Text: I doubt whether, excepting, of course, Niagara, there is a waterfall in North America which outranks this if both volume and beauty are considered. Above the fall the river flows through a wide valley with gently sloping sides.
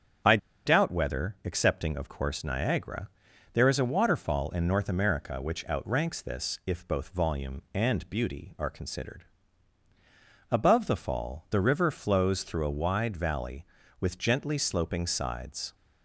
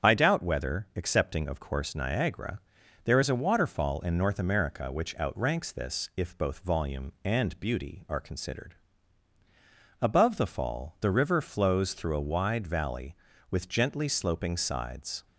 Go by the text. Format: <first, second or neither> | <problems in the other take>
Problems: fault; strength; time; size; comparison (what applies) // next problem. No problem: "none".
second | starts louder than the rest; strong; until 1.6 s; 8 dB; strong in the second // pauses between "I" and "doubt"; slight; at 0.3 s; 0.29 s long